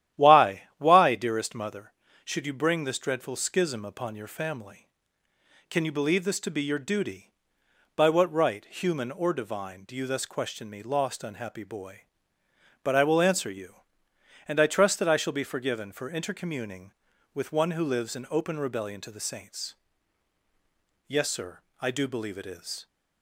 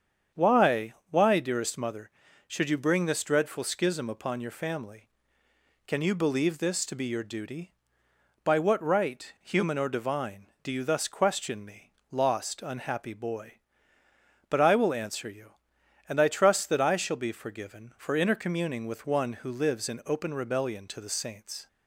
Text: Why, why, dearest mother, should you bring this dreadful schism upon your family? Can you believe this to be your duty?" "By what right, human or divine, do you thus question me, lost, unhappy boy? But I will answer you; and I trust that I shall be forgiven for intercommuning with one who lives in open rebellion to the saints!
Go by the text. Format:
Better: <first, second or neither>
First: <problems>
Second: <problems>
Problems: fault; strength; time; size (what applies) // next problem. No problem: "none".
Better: second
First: starts louder than the rest; strong; until 1.2 s; 12 dB // goes on to say "Yes sir I do believe it is"; strong; from 21.0 s on; 1.7 s long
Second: starts louder than the rest; strong; until 1.5 s; 7.5 dB